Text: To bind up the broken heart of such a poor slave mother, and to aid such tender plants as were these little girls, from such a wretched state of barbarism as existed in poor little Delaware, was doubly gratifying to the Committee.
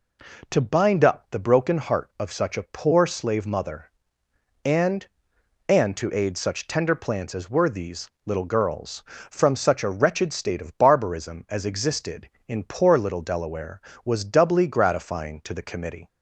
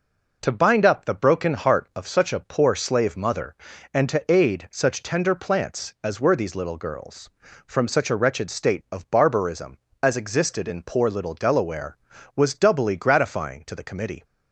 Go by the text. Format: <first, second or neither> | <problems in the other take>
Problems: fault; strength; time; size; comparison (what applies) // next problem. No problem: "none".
second | says "and" twice; at 5.6 s // pauses between "these" and "little"; slight; at 8.0 s; 0.16 s long